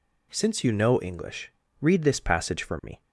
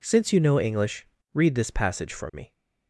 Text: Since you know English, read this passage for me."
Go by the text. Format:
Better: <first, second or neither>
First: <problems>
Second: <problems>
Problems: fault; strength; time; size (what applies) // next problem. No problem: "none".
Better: neither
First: none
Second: none